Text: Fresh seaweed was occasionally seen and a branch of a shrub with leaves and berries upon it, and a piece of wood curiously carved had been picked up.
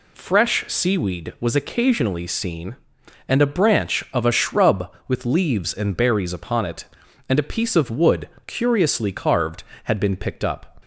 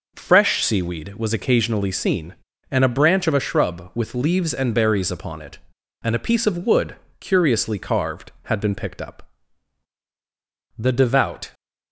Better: first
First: pauses between "wood" and "curiously"; slight; at 8.2 s; 0.16 s long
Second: pauses between "wood" and "curiously"; slight; at 6.9 s; 0.24 s long // goes on to say "The devout"; noticeable; from 10.7 s on; 0.76 s long

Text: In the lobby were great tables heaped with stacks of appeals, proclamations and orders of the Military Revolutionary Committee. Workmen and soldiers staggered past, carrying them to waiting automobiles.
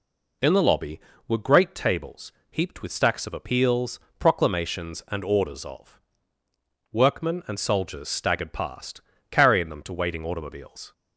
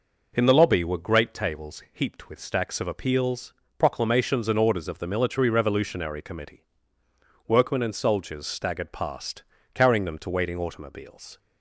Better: second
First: pauses between "tables" and "heaped"; slight; at 2.3 s; 0.20 s long // skips "the Military Revolutionary Committee"; at 6.4 s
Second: none

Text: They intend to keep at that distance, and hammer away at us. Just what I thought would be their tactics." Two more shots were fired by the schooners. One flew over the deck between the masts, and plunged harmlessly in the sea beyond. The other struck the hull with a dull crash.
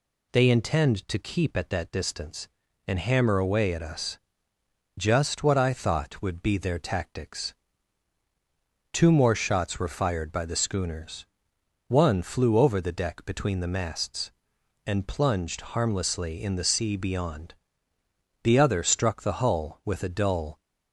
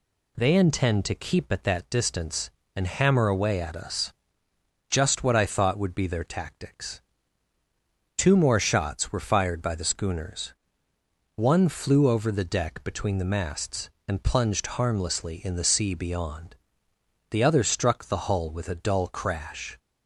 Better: second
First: stops before "crash"; at 20.5 s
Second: none

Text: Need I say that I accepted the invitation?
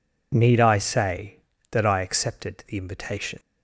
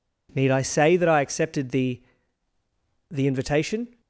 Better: first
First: none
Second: says "the" twice; at 3.1 s

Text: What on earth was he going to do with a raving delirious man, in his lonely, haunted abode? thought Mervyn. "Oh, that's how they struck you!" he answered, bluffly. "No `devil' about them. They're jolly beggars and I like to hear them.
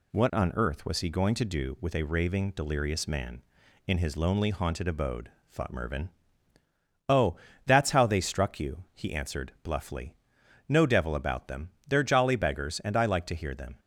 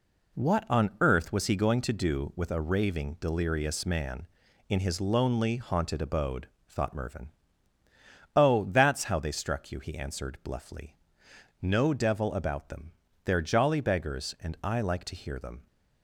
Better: neither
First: none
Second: none

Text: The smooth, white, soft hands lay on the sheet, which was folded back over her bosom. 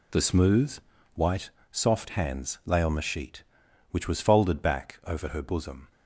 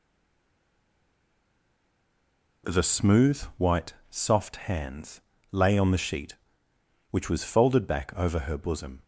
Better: first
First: none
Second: stays silent before the first word; strong; until 2.6 s; 2.6 s long // pauses between "hands" and "lay"; slight; at 5.2 s; 0.30 s long

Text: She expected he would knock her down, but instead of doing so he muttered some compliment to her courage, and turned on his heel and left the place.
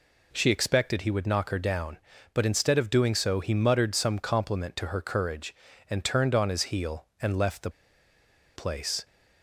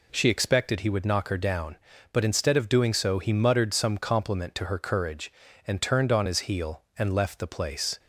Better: second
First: pauses between "the" and "place"; noticeable; at 7.6 s; 0.85 s long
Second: none

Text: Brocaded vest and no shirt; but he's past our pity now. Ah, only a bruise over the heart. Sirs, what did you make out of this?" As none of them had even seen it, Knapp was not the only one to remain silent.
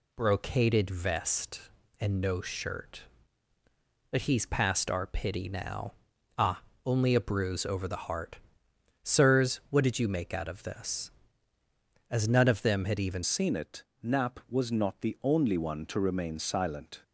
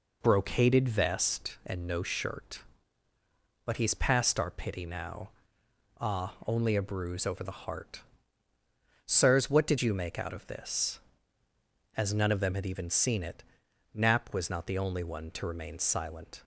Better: second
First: changes voice at "seen"; from 13.2 s on; 3.8 s long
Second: none

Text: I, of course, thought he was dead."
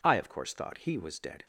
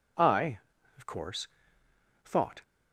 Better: first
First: none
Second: stops before "he was dead"; at 2.6 s

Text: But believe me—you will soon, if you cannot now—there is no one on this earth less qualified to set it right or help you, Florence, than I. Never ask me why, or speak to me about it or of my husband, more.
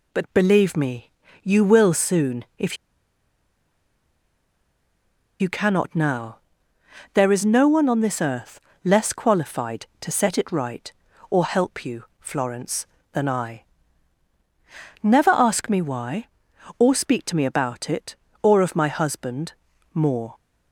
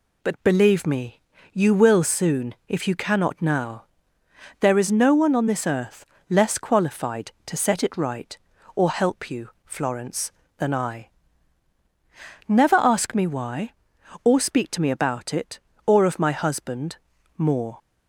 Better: second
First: pauses between "if" and "you"; strong; at 2.7 s; 2.6 s long // pauses between "earth" and "less"; slight; at 8.5 s; 0.24 s long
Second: pauses between "earth" and "less"; slight; at 6.0 s; 0.24 s long

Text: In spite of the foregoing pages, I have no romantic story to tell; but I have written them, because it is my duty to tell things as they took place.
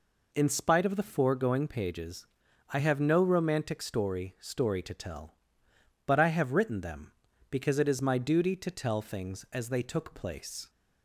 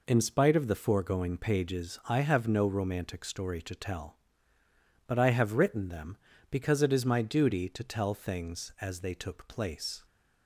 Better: second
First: says "story" twice; at 4.3 s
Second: none

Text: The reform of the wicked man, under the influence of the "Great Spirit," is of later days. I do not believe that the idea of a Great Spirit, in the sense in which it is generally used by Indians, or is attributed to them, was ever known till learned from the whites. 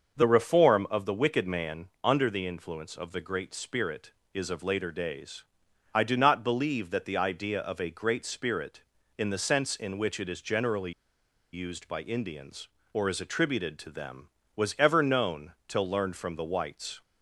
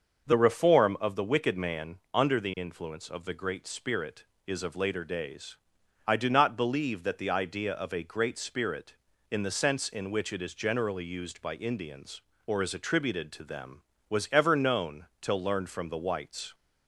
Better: second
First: starts louder than the rest; until 1.2 s; 6.5 dB // pauses between "generally" and "used"; noticeable; at 10.9 s; 0.61 s long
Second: starts louder than the rest; until 1.3 s; 6.5 dB

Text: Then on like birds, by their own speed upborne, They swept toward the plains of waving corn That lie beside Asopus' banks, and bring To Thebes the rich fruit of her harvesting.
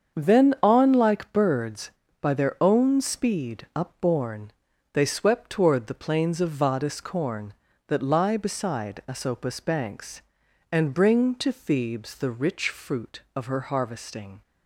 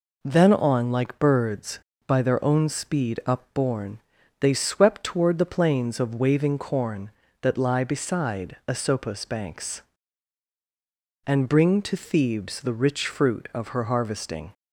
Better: second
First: starts louder than the rest; until 1.2 s; 7 dB // says "vadis" for "waving"; at 6.5 s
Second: none

